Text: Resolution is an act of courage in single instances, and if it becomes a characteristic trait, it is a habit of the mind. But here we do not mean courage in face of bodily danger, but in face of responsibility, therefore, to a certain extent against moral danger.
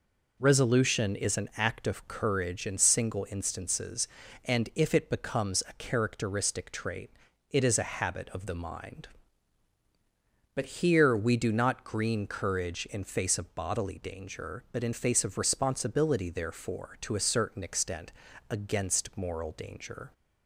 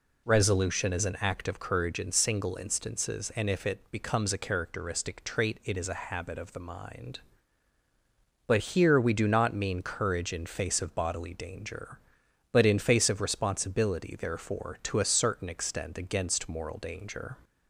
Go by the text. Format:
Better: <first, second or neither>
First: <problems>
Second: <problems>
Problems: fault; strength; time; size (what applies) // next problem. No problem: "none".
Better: second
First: says "green" for "mean"; at 11.8 s // pauses between "extent" and "against"; at 18.1 s; 0.40 s long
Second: none